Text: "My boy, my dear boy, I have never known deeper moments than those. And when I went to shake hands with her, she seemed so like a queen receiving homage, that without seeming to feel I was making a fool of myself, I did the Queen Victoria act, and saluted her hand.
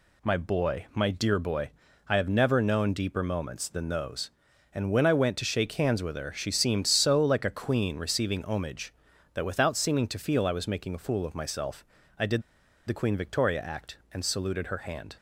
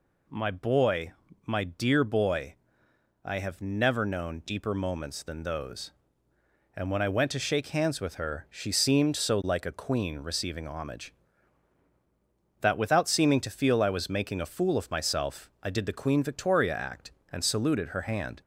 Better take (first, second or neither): second